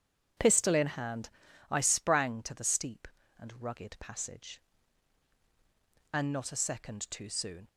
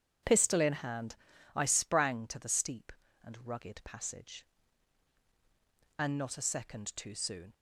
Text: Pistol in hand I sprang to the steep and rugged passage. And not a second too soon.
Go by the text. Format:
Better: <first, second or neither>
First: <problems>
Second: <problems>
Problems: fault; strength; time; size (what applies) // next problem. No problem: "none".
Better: neither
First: pauses between "hand" and "I"; at 1.2 s; 0.38 s long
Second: pauses between "hand" and "I"; at 1.1 s; 0.36 s long